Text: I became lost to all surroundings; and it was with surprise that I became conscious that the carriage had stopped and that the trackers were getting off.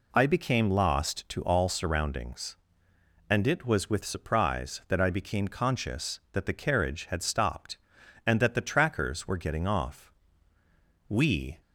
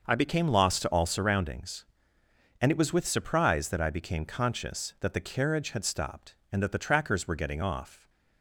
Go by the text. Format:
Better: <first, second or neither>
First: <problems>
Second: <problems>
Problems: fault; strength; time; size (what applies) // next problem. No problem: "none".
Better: second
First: goes on to say "We"; from 11.0 s on; 0.52 s long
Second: none